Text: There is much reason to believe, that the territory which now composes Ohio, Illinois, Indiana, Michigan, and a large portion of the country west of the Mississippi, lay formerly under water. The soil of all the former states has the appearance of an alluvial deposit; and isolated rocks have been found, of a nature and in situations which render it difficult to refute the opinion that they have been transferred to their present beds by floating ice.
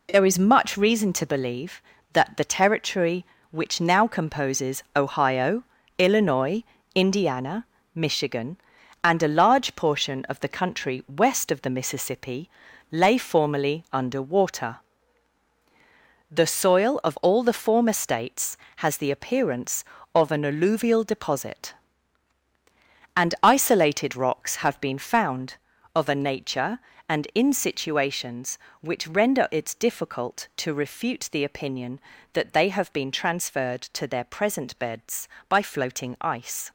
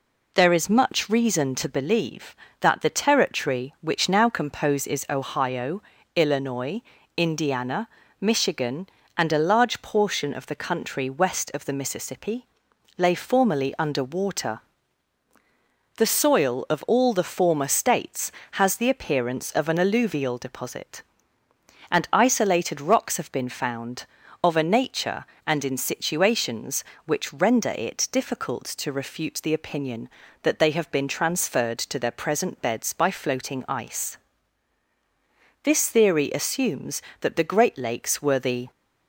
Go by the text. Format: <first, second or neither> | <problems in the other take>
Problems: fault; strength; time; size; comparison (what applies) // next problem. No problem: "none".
first | goes on to say "This theory assumes that the Great Lakes were the"; strong; from 35.6 s on; 3.0 s long